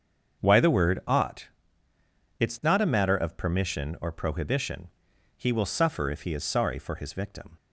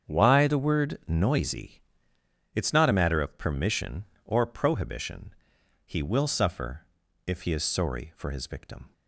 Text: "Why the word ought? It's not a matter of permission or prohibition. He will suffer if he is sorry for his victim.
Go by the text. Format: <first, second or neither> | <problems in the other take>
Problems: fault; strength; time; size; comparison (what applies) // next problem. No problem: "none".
first | starts louder than the rest; strong; until 1.1 s; 7.5 dB; also in the first // says "noisy" for "ought"; at 1.0 s // pauses between "suffer" and "if"; at 6.8 s; 0.40 s long